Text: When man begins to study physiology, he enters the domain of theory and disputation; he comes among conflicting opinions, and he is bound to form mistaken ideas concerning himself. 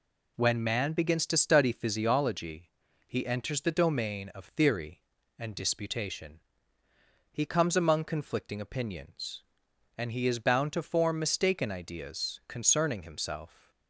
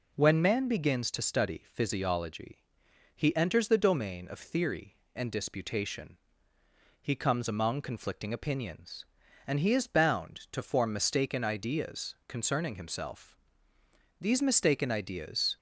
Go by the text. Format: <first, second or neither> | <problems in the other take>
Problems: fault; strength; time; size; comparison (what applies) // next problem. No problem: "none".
first | goes on to say "These mistaken ideas"; from 14.2 s on; 1.3 s long